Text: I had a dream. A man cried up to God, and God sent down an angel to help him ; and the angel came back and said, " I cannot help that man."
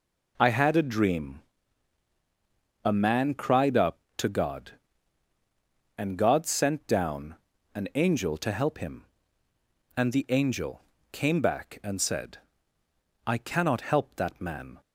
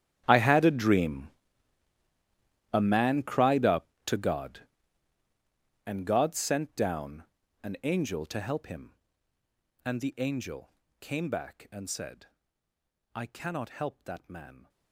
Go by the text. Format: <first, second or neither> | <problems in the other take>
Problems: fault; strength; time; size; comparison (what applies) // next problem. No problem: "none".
first | gets quieter; strong; throughout; 27 dB // pauses between "down" and "an"; slight; at 7.2 s; 0.36 s long; slight in the first // pauses between "angel" and "came"; slight; at 10.6 s; 0.32 s long; slight in the first